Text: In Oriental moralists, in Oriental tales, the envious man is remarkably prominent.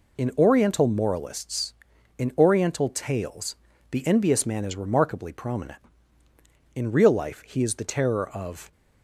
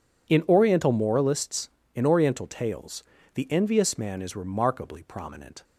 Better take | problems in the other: second | goes on to say "In real life he is the terror of"; strong; from 6.7 s on; 1.9 s long

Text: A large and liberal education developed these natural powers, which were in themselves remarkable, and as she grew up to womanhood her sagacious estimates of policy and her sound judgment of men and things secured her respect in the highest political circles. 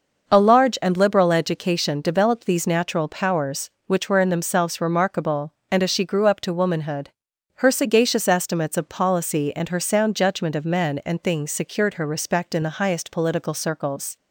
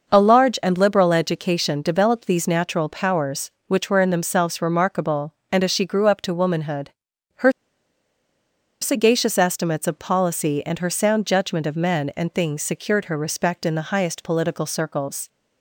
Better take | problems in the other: first | pauses between "womanhood" and "her"; noticeable; at 6.9 s; 0.50 s long; noticeable in the first // pauses between "her" and "sagacious"; strong; at 7.5 s; 1.3 s long

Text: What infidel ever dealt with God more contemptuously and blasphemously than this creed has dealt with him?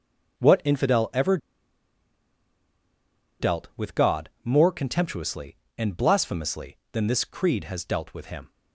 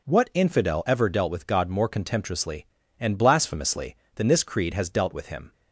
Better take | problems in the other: second | pauses between "ever" and "dealt"; strong; at 1.3 s; 2.0 s long // pauses between "God" and "more"; slight; at 4.2 s; 0.16 s long

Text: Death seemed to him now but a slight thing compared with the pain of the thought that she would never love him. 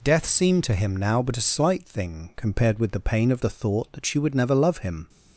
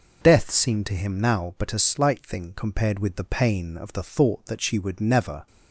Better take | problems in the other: first | stops before "love him"; at 5.4 s

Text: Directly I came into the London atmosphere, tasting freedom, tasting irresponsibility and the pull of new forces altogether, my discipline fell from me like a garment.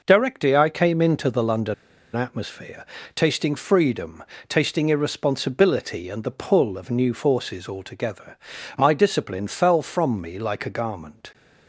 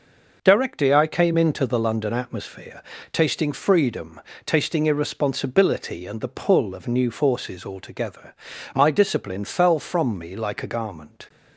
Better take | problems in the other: second | pauses between "London" and "atmosphere"; at 1.7 s; 0.40 s long

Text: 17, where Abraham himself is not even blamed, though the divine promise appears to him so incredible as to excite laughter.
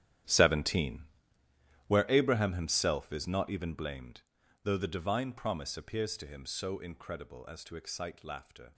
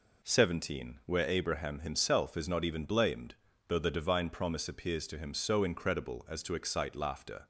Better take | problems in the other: second | gets quieter; strong; throughout; 16 dB

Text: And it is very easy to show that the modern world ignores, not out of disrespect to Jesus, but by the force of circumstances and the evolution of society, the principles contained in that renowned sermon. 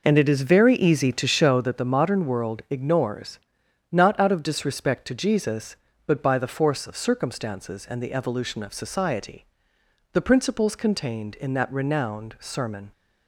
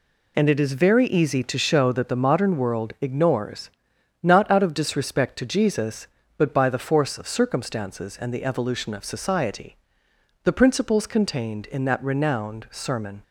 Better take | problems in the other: second | starts louder than the rest; noticeable; until 1.7 s; 5 dB

